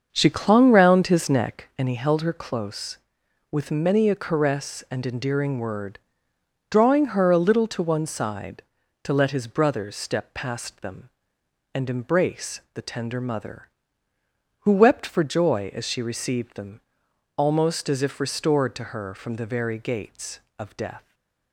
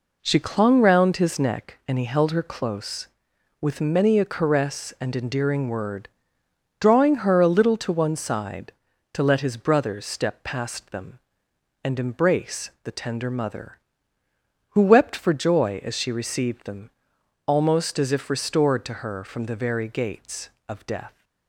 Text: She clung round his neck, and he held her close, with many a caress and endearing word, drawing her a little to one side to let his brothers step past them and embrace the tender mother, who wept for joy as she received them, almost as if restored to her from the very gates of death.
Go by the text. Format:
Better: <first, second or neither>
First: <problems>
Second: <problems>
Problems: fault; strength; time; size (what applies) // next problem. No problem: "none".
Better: second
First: starts louder than the rest; until 1.9 s; 6.5 dB // stays silent after the last word; slight; from 20.9 s on; 0.6 s long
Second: none